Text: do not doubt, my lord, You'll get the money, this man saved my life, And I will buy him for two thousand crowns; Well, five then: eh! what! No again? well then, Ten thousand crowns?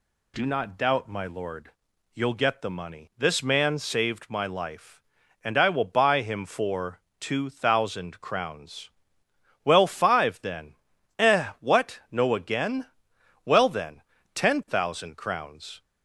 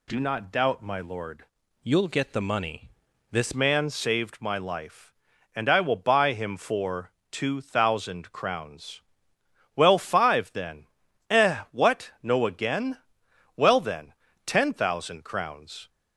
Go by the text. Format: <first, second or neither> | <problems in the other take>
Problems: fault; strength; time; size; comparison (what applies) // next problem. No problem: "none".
first | changes voice from "You'll" to "this"; from 1.8 to 3.5 s; 1.7 s long // pauses between "for" and "two"; slight; at 7.1 s; 0.22 s long; slight in the first